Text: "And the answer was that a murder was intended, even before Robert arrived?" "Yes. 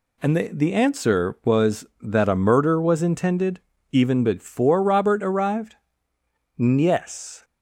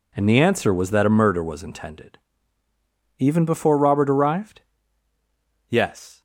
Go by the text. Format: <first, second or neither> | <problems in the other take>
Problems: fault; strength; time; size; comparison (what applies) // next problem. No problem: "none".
second | says "the" twice; at 0.5 s